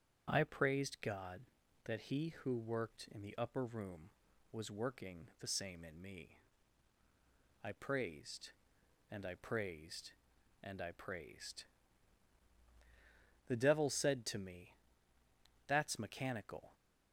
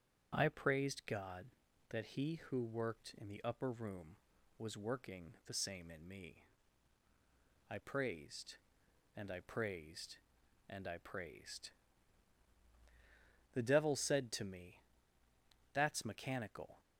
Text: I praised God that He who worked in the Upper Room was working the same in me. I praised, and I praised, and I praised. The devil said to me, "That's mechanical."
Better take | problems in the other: neither | none

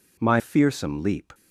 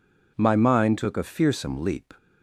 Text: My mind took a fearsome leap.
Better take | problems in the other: second | skips "mind took a"; at 0.3 s

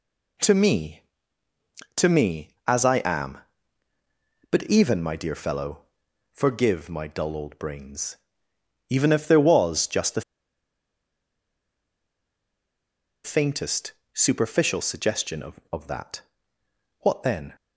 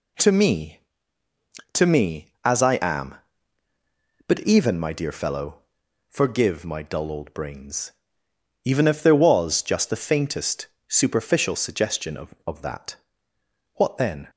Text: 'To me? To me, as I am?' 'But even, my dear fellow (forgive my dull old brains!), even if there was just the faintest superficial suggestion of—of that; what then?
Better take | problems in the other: second | pauses between "the" and "faintest"; strong; at 10.2 s; 3.0 s long // pauses between "faintest" and "superficial"; slight; at 13.9 s; 0.20 s long; slight in the second

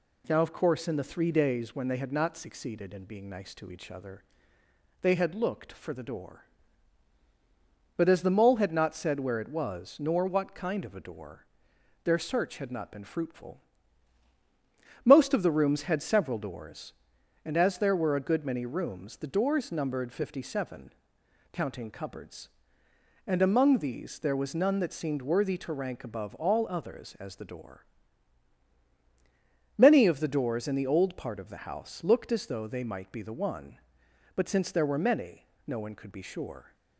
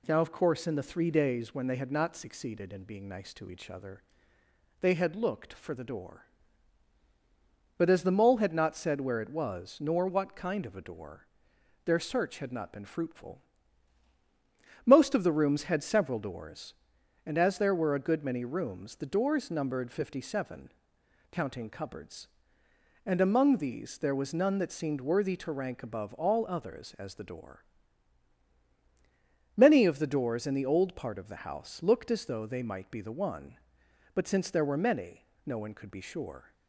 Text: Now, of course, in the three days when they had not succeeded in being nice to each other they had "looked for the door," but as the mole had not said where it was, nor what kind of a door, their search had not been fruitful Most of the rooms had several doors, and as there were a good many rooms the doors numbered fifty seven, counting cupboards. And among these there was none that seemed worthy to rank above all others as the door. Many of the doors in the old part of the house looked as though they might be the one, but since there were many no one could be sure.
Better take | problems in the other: neither | pauses between "other" and "they"; noticeable; the same in both // pauses between "fruitful" and "Most"; strong; the same in both // pauses between "many" and "no"; slight; the same in both

